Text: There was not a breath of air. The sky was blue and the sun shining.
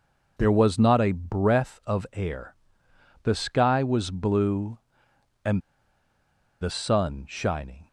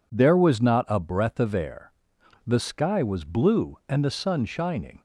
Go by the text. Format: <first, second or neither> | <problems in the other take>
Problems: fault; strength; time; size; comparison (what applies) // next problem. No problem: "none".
second | pauses between "and" and "the"; at 5.6 s; 1.0 s long